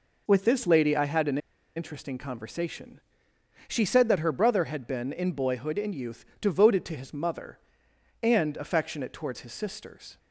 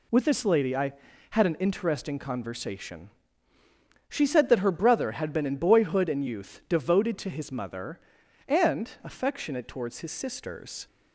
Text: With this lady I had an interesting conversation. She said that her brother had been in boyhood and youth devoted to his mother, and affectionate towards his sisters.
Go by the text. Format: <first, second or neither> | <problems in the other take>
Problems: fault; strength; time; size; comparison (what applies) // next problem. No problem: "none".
second | pauses between "an" and "interesting"; at 1.3 s; 0.38 s long // pauses between "youth" and "devoted"; slight; at 6.2 s; 0.16 s long